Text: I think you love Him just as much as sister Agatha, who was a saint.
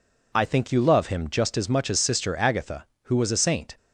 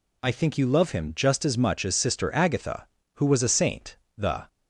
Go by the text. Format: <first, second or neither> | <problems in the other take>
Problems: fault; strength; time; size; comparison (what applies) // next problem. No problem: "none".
first | goes on to say "The"; slight; from 4.1 s on; 0.32 s long